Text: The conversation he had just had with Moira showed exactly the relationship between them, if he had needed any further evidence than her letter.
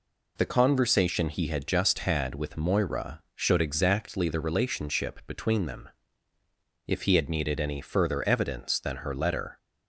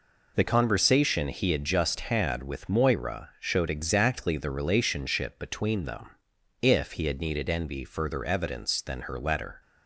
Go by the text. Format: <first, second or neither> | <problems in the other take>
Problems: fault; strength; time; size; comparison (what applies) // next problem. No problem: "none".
first | says "envy" for "any"; at 7.4 s